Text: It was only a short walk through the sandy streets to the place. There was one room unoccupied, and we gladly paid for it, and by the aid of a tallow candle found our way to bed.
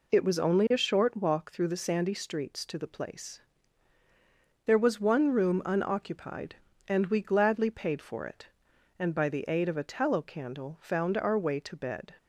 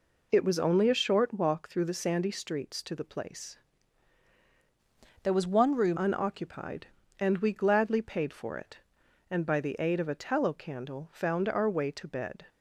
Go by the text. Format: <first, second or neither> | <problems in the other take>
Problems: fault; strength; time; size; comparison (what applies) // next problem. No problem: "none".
first | changes voice from "There" to "room"; from 5.2 to 5.9 s; 0.7 s long